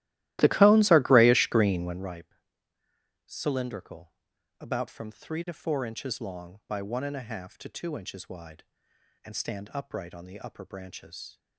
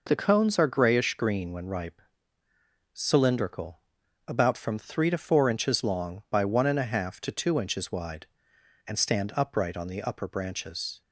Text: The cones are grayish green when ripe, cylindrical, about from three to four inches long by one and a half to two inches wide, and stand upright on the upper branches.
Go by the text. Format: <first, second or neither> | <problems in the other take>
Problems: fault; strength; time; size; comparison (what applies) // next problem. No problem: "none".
second | starts louder than the rest; strong; until 2.2 s; 15.5 dB